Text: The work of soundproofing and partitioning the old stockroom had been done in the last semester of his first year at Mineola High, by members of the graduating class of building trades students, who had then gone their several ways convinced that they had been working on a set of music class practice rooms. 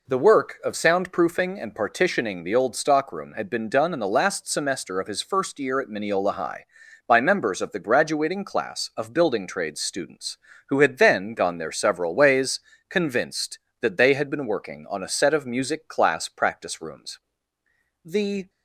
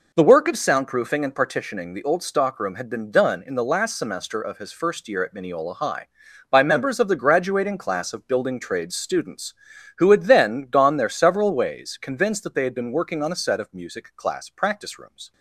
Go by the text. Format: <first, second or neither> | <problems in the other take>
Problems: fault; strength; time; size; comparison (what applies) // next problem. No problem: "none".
second | pauses between "ways" and "convinced"; slight; at 12.5 s; 0.28 s long // goes on to say "The"; slight; from 18.0 s on; 0.46 s long